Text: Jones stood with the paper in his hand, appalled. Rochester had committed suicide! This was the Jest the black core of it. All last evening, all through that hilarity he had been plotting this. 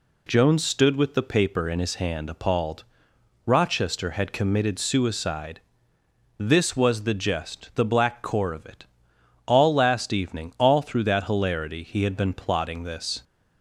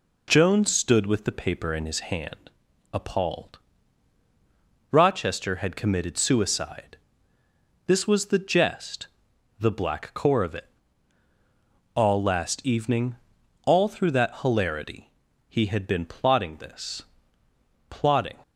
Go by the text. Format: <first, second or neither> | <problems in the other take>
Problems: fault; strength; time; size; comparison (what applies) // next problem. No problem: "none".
first | pauses between "Jest" and "the"; noticeable; at 9.0 s; 0.52 s long // pauses between "hilarity" and "he"; at 15.1 s; 0.38 s long // goes on to say "Plotting"; from 17.8 s on; 0.50 s long